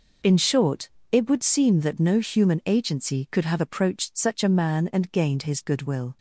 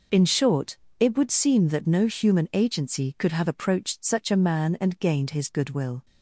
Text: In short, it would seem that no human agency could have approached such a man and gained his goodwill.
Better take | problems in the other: neither | none

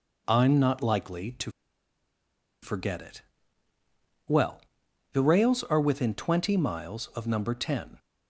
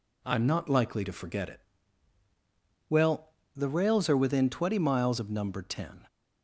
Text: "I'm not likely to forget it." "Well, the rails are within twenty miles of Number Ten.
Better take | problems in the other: second | pauses between "to" and "forget"; at 1.5 s; 1.1 s long

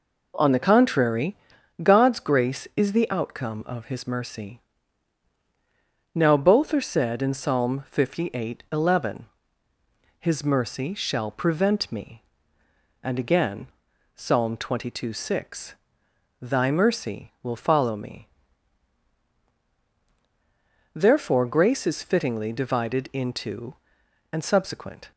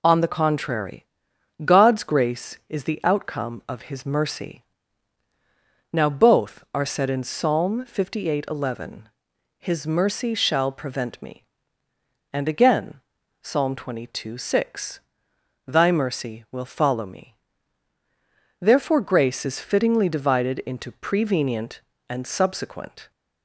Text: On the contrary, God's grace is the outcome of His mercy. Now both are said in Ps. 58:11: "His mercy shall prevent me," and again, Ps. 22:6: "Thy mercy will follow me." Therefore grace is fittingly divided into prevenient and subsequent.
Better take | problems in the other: second | skips "prevenient"; at 24.0 s

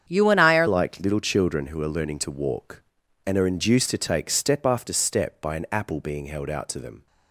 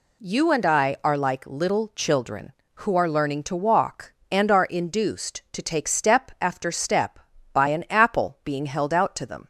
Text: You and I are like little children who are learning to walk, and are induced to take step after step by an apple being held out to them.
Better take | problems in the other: second | starts louder than the rest; strong; until 1.0 s; 8 dB // changes voice at "like"; from 0.6 s on; 6.4 s long

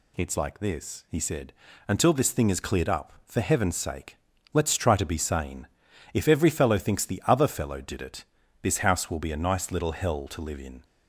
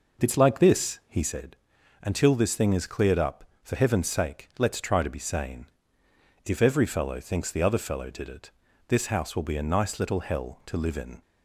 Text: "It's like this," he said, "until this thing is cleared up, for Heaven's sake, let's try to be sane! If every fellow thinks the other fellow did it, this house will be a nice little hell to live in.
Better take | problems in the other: first | starts louder than the rest; noticeable; until 1.4 s; 5 dB

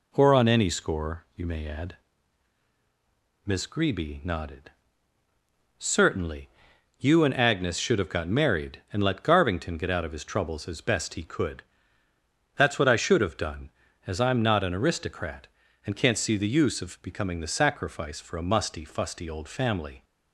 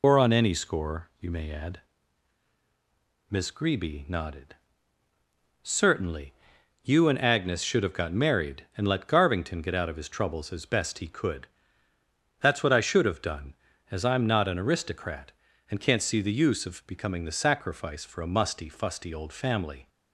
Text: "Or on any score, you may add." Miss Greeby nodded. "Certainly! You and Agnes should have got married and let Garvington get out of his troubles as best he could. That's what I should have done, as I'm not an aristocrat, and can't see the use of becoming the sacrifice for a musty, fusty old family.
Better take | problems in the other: first | loses the start of "Or"; at 0.0 s; 55 ms

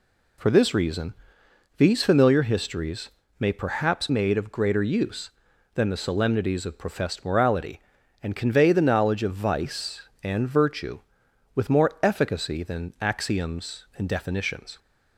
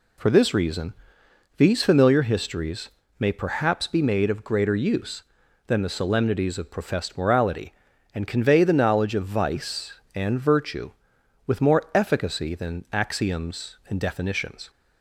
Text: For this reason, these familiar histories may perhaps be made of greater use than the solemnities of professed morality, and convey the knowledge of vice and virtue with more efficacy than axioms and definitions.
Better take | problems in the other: second | pauses between "histories" and "may"; slight; at 3.0 s; 0.32 s long; slight in the second // skips "be"; at 4.0 s

